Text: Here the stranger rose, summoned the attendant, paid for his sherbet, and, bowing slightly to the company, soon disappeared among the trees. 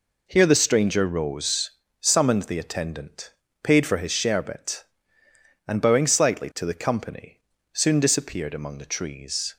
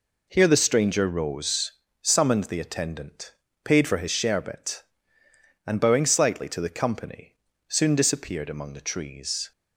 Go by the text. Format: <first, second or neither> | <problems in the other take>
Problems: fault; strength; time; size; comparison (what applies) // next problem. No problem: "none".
neither | none